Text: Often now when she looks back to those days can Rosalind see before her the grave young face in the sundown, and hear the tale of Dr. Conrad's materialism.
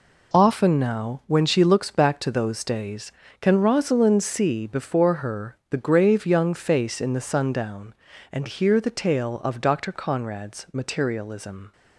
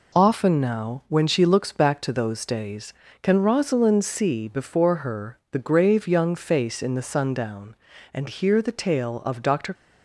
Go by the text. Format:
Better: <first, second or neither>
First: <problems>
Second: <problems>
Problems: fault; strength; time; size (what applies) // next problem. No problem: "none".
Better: first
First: none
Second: stops before "Conrad's materialism"; at 9.7 s